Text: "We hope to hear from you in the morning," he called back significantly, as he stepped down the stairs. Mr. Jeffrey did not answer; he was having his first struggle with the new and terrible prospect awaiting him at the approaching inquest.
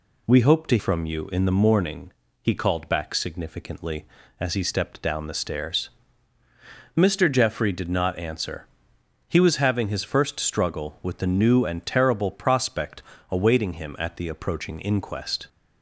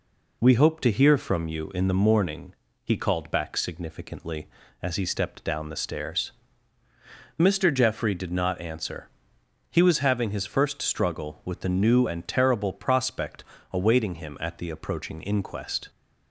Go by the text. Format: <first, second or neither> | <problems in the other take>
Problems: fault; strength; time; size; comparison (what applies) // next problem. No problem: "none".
second | skips "hear"; at 0.7 s // pauses between "prospect" and "awaiting"; slight; at 13.0 s; 0.26 s long; slight in the second